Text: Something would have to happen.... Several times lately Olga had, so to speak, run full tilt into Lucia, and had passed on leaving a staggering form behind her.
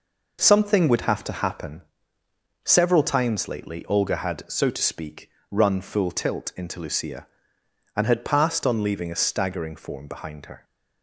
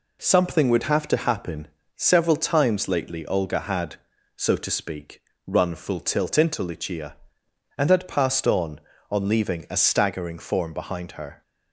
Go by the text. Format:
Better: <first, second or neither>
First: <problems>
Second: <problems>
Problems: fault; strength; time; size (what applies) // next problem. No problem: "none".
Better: first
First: none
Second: says "on" twice; at 9.1 s